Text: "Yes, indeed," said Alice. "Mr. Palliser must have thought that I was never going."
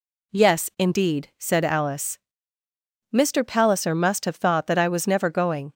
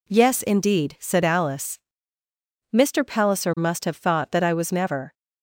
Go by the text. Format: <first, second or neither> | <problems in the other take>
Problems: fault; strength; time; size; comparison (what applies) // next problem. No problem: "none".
first | stops before "going"; at 5.1 s